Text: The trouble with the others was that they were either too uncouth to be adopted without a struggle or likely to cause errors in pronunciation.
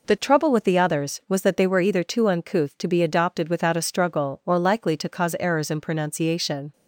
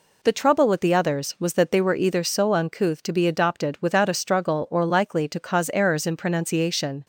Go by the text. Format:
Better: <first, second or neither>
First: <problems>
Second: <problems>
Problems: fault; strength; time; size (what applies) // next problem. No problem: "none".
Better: first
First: none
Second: says "so" for "too"; at 2.2 s